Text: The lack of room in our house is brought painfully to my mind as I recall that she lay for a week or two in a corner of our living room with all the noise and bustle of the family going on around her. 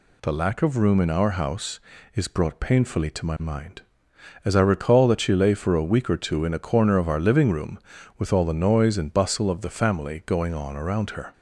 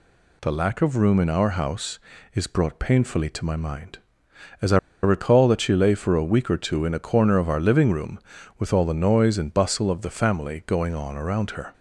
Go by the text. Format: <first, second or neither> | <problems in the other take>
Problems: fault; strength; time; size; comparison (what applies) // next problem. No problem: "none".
first | pauses between "I" and "recall"; slight; at 4.7 s; 0.26 s long